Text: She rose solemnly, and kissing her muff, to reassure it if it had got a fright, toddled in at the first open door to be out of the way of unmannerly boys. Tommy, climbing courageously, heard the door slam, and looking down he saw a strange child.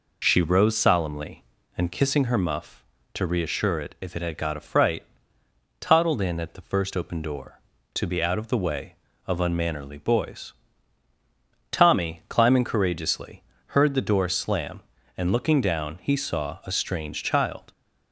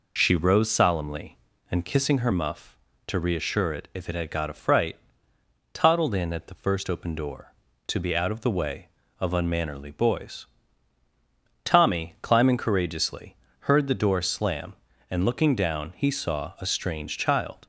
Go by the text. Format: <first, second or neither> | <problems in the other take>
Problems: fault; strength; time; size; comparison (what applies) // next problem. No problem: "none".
neither | none